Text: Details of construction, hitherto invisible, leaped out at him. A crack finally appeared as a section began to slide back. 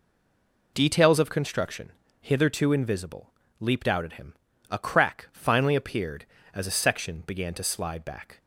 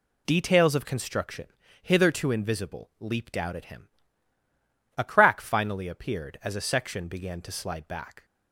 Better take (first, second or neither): second